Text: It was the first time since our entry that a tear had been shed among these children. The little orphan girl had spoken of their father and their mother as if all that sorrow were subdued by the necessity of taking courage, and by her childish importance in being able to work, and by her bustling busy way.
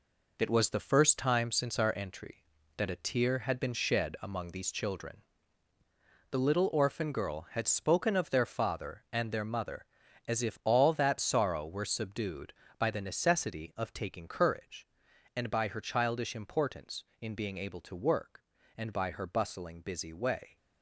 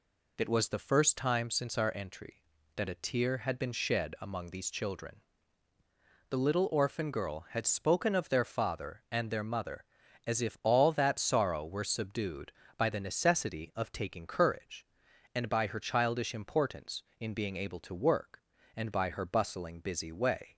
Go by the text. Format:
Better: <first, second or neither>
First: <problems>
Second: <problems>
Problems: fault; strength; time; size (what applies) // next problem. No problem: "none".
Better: second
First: gets quieter; strong; throughout; 7.5 dB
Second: none